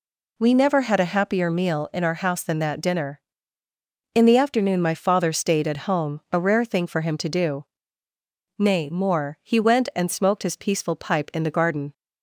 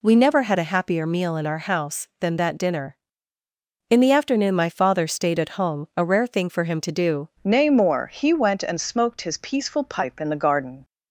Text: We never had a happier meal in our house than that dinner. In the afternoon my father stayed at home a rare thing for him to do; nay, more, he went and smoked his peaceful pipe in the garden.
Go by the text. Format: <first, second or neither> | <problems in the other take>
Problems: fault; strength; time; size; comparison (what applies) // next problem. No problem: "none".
first | changes voice at "nay"; from 7.4 s on; 3.4 s long